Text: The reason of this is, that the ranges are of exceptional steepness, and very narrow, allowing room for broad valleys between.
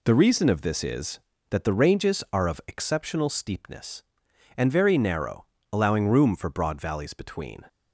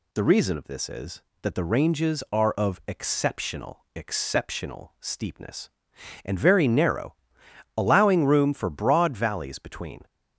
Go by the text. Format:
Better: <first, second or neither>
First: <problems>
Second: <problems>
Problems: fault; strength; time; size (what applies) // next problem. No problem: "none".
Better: first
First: none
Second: says "exceptional" twice; at 3.9 s